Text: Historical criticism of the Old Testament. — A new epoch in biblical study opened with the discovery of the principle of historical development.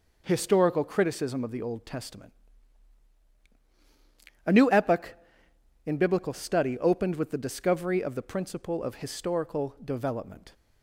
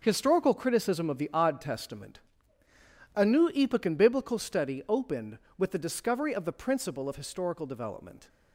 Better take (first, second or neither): first